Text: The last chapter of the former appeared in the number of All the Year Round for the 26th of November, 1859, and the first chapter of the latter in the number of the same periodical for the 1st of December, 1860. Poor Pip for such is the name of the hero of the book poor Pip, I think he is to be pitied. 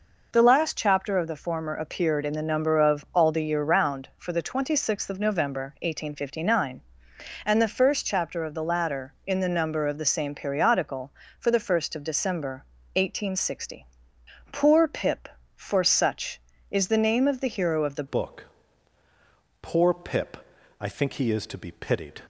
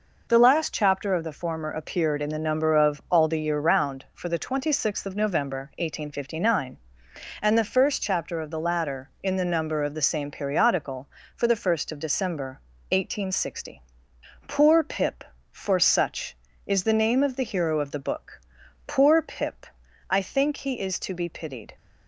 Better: second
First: changes voice at "book"; from 18.0 s on; 4.2 s long // pauses between "book" and "poor"; at 18.4 s; 1.1 s long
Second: pauses between "book" and "poor"; at 18.4 s; 0.44 s long

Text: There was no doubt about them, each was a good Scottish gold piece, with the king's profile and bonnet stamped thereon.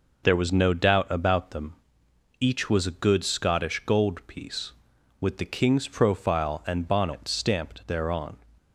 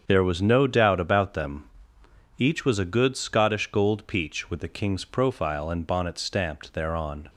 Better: first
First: none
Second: starts louder than the rest; strong; until 1.0 s; 7.5 dB // says "peach" for "piece"; at 4.0 s

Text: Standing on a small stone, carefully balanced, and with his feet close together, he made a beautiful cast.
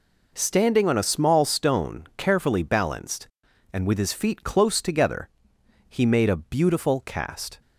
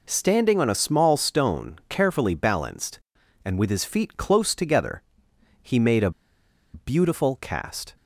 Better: first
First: none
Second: pauses between "a" and "beautiful"; noticeable; at 6.1 s; 0.63 s long

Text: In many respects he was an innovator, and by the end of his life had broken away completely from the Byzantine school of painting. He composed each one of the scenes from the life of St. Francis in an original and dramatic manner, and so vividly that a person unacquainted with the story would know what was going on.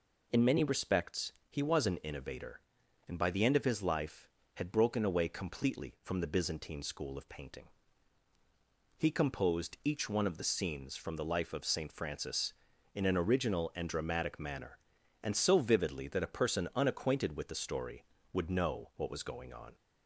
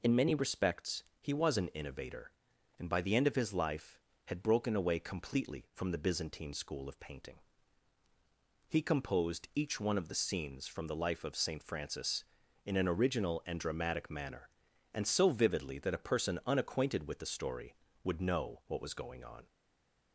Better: first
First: pauses between "respects" and "he"; slight; at 1.3 s; 0.16 s long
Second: pauses between "respects" and "he"; slight; at 1.0 s; 0.16 s long // stays silent after the last word; slight; from 19.4 s on; 0.7 s long

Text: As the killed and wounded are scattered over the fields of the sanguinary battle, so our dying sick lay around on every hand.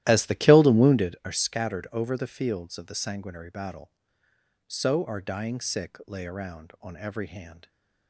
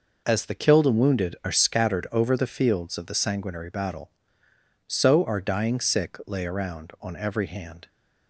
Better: second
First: starts louder than the rest; strong; until 1.2 s; 14 dB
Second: none

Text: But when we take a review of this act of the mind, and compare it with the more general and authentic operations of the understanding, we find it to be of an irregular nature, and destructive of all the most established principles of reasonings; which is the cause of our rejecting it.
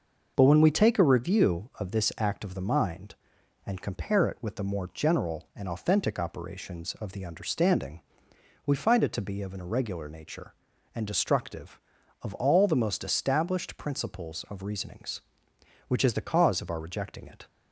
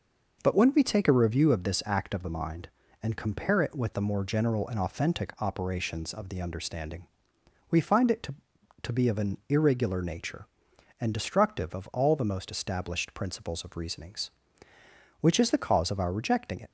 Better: first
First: none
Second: says "to" twice; at 8.8 s

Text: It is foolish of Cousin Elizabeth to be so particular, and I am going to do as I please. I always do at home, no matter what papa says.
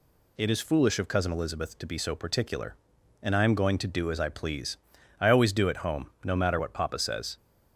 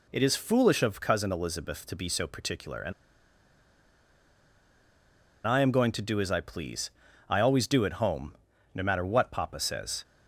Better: first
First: none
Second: pauses between "and" and "I"; strong; at 2.9 s; 2.5 s long

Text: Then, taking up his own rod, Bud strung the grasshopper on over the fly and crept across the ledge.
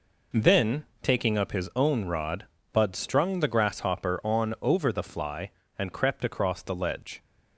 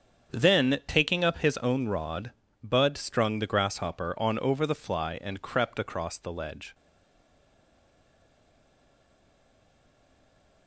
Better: first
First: none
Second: starts louder than the rest; strong; until 1.3 s; 7.5 dB // stays silent after the last word; strong; from 6.7 s on; 3.9 s long

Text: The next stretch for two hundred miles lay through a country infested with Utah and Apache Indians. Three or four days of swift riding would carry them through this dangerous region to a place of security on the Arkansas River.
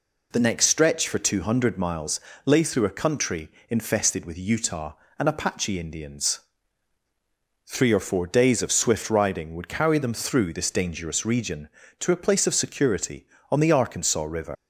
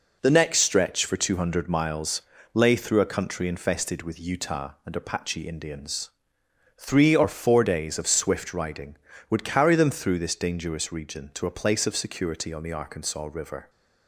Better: second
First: pauses between "miles" and "lay"; slight; at 2.1 s; 0.28 s long // pauses between "country" and "infested"; slight; at 3.4 s; 0.18 s long // leaves "River" unfinished; at 14.5 s; 160 ms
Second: pauses between "miles" and "lay"; slight; at 2.2 s; 0.30 s long

